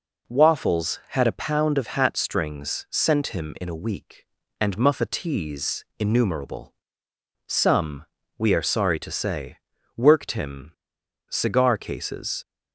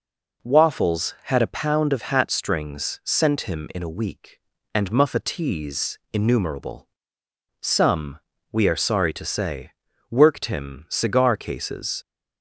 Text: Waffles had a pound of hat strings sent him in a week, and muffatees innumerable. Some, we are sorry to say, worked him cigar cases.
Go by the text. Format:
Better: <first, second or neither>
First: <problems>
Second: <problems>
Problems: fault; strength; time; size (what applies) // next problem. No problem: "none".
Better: second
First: pauses between "him" and "cigar"; noticeable; at 10.7 s; 0.59 s long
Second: none